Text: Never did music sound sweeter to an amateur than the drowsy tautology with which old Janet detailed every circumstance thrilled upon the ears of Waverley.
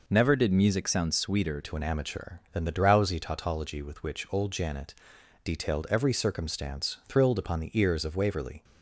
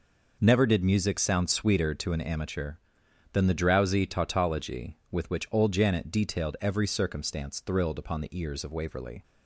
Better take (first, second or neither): second